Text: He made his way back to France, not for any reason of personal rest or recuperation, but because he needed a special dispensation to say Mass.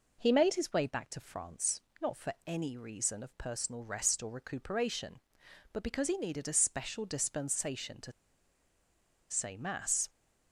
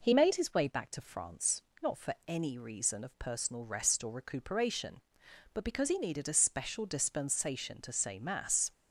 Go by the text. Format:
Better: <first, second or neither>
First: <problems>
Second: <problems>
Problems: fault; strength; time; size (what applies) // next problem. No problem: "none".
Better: second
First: pauses between "to" and "say"; at 8.1 s; 1.1 s long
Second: none